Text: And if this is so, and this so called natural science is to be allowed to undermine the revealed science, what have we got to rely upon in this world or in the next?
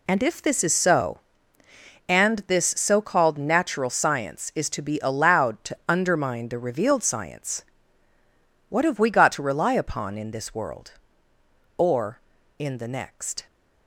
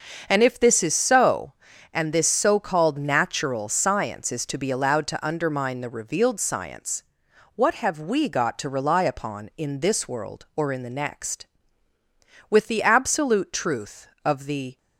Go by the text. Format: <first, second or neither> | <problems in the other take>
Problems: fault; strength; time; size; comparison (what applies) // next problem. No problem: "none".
first | starts louder than the rest; until 1.3 s; 6.5 dB // goes on to say "With the absolute truth of the"; strong; from 12.4 s on; 2.2 s long